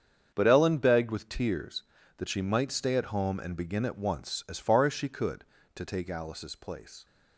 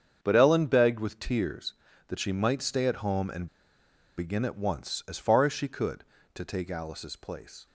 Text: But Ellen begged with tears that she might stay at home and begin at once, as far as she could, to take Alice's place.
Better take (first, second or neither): first